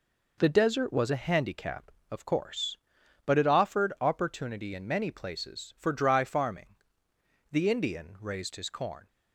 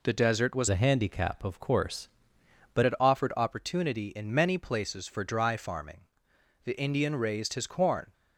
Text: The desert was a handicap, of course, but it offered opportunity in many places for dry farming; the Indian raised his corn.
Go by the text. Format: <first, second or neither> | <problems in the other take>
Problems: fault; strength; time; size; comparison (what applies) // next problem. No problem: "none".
first | changes voice from "a" to "but"; from 0.7 to 2.8 s; 2.1 s long